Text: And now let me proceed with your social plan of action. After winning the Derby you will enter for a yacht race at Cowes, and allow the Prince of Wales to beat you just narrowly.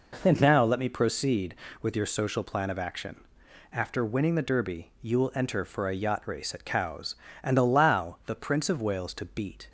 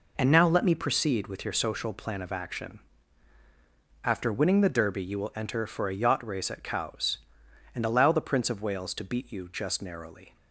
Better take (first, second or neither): second